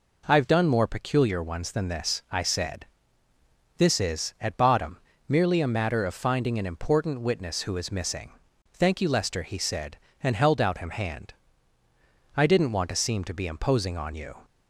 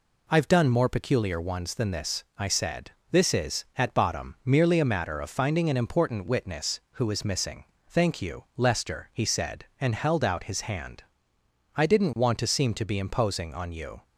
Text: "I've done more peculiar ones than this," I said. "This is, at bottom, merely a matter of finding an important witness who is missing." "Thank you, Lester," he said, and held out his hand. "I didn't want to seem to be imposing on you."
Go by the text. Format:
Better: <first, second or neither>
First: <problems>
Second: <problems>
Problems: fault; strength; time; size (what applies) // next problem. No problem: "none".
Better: second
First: says "him" for "his"; at 10.7 s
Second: none